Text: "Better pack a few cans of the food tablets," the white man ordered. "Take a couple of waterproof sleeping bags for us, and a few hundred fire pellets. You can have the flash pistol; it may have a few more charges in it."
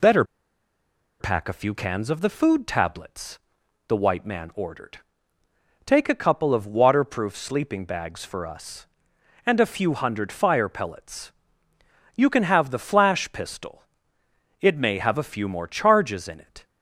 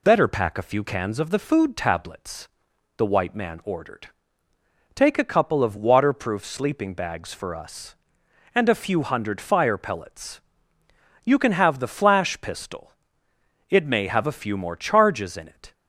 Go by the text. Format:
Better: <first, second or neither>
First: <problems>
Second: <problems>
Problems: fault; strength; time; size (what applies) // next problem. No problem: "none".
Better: second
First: pauses between "Better" and "pack"; noticeable; at 0.2 s; 0.96 s long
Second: none